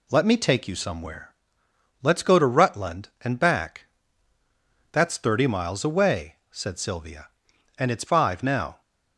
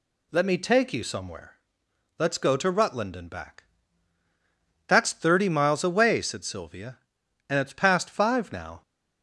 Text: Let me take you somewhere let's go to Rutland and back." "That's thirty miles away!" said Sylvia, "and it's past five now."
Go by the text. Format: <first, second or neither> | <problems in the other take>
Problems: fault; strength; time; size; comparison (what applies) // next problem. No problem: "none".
second | pauses between "somewhere" and "let's"; noticeable; at 1.3 s; 0.70 s long; noticeable in the second // skips "past"; at 8.0 s